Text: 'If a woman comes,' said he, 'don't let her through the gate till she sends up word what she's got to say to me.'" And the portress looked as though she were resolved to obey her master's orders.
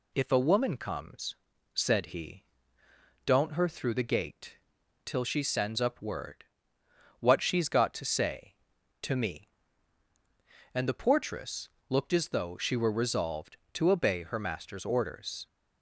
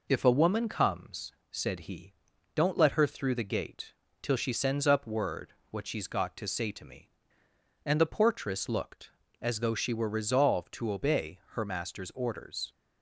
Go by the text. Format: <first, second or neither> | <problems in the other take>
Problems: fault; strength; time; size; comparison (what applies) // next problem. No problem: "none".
second | skips "let"; at 3.5 s // pauses between "gate" and "till"; noticeable; at 4.5 s; 0.48 s long; slight in the second // pauses between "word" and "what"; noticeable; at 6.4 s; 0.76 s long; slight in the second // pauses between "portress" and "looked"; slight; at 11.7 s; 0.18 s long